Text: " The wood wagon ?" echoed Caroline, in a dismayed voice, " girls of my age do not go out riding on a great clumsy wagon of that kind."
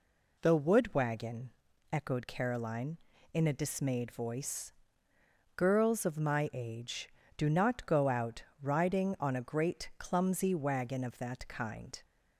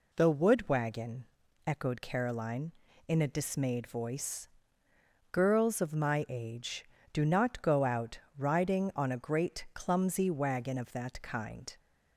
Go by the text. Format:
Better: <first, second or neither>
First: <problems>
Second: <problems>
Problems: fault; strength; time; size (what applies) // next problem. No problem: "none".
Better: neither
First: pauses between "out" and "riding"; slight; at 8.4 s; 0.18 s long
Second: pauses between "out" and "riding"; slight; at 8.1 s; 0.18 s long